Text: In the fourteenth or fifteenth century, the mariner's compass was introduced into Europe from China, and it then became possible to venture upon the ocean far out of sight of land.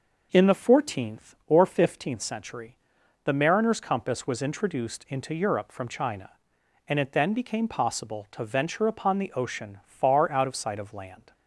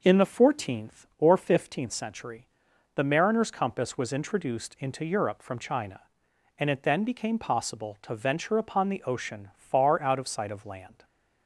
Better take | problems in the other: neither | none

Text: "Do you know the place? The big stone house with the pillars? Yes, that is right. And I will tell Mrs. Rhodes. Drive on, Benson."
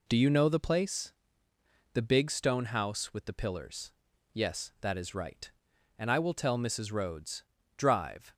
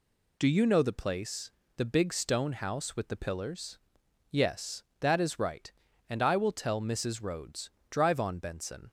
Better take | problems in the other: second | stops before "on Benson"; at 8.3 s

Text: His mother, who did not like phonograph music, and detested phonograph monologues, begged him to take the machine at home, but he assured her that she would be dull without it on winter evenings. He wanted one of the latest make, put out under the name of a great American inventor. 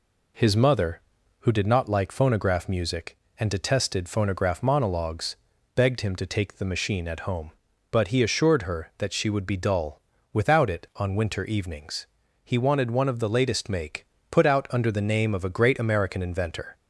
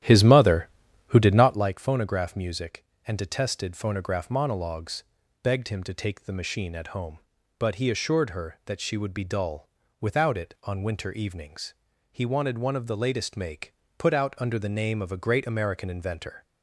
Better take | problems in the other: first | starts louder than the rest; strong; until 1.7 s; 11.5 dB // pauses between "dull" and "without"; slight; at 9.6 s; 0.32 s long; slight in the first

